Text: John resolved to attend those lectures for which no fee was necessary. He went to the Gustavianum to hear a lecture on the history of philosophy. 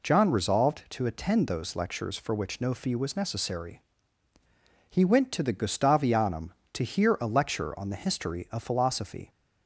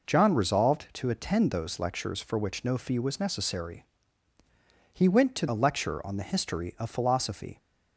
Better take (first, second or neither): first